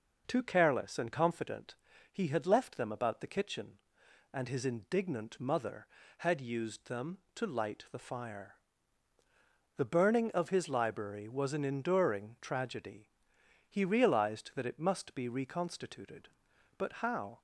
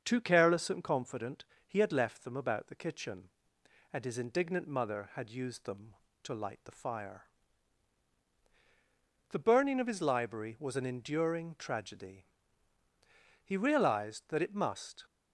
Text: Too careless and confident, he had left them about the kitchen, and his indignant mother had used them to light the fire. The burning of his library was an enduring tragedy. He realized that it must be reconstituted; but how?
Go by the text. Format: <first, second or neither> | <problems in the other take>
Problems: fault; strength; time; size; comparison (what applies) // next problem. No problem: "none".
first | starts louder than the rest; until 1.0 s; 6.5 dB // stops before "be reconstituted but how"; at 15.0 s